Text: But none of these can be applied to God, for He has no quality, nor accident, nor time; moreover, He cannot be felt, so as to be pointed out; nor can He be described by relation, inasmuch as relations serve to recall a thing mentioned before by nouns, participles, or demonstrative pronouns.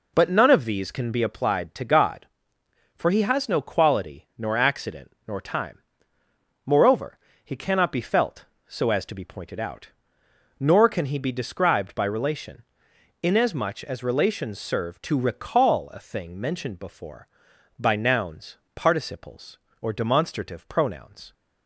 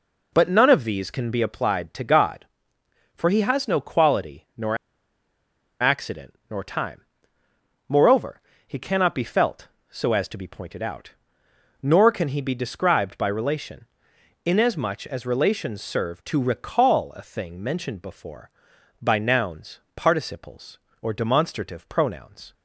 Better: first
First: none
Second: pauses between "nor" and "accident"; at 4.7 s; 1.0 s long

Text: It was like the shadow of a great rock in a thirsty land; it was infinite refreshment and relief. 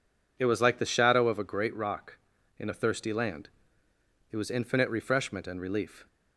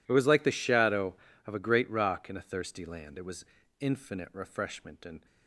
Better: first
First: none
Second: pauses between "was" and "infinite"; slight; at 3.4 s; 0.36 s long // stops before "relief"; at 5.2 s

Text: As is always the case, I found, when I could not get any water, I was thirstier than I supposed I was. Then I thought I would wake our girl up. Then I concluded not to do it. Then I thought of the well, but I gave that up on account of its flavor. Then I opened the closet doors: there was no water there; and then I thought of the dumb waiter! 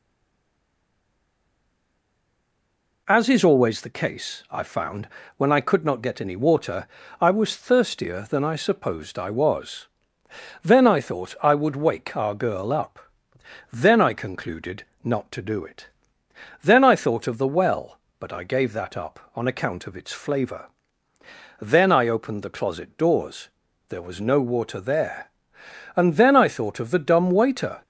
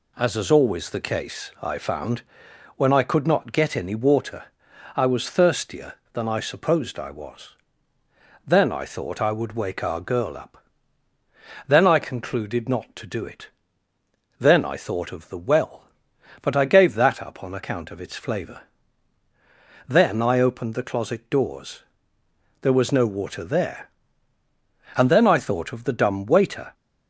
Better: second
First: stays silent before the first word; strong; until 3.0 s; 3.0 s long // pauses between "concluded" and "not"; slight; at 14.8 s; 0.18 s long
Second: none

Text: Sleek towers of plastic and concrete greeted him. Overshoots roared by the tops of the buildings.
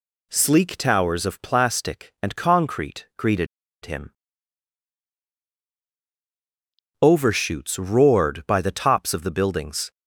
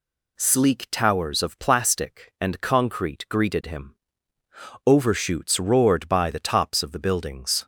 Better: second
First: pauses between "greeted" and "him"; at 3.4 s; 0.37 s long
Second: none

